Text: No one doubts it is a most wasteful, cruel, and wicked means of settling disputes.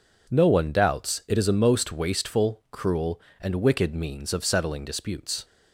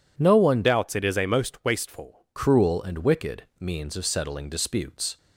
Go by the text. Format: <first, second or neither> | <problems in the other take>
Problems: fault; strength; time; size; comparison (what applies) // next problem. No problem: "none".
first | changes voice from "doubts" to "wasteful"; from 0.6 to 2.2 s; 1.6 s long // pauses between "wicked" and "means"; slight; at 3.4 s; 0.16 s long